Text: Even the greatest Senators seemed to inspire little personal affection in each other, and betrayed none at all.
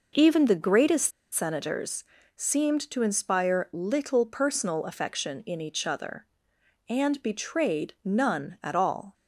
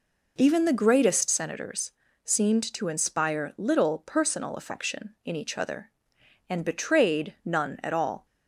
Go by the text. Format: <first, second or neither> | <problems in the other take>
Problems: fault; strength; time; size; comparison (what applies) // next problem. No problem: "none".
second | pauses between "greatest" and "Senators"; slight; at 1.1 s; 0.21 s long // pauses between "Senators" and "seemed"; slight; at 2.0 s; 0.32 s long; slight in the second